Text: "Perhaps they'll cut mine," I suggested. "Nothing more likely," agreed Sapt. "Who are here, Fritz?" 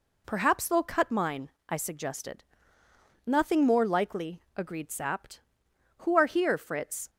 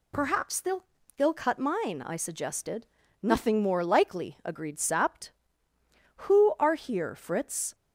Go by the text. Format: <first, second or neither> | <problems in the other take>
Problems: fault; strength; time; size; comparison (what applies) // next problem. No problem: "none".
first | says "they'll" twice; at 1.1 s